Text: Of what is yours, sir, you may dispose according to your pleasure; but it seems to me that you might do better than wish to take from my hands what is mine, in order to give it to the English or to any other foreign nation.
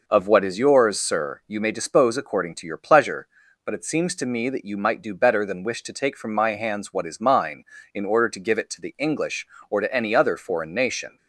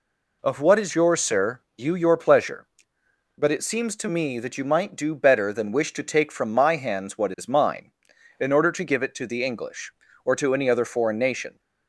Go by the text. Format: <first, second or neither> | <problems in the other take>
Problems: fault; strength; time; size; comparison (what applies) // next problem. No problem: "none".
first | skips "may dispose according to"; at 1.9 s